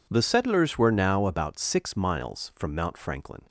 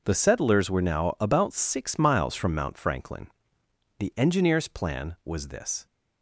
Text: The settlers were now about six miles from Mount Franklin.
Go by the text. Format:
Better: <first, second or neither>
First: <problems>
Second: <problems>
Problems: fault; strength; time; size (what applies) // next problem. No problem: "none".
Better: first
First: none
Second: goes on to say "The engineer's plan was this"; strong; from 3.9 s on; 1.8 s long